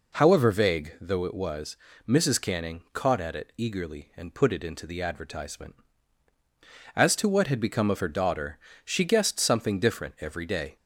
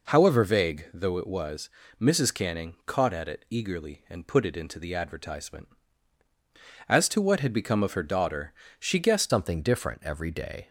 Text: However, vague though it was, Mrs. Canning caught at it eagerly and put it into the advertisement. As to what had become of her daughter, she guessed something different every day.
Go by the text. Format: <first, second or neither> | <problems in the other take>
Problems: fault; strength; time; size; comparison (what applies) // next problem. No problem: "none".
first | changes voice at "something"; from 9.2 s on; 1.4 s long